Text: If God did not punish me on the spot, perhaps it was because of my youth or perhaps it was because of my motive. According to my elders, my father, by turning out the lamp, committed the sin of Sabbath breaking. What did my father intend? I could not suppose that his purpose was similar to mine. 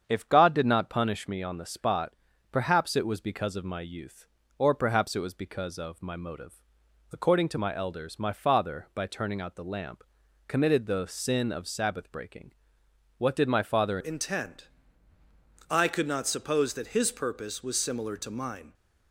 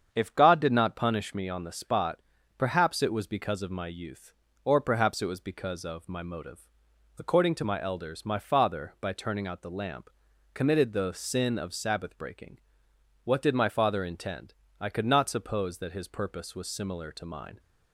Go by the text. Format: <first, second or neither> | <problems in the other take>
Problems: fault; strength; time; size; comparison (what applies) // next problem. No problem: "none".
second | starts louder than the rest; strong; until 1.0 s; 7.5 dB; strong in the second // changes voice at "intend"; from 13.9 s on; 4.8 s long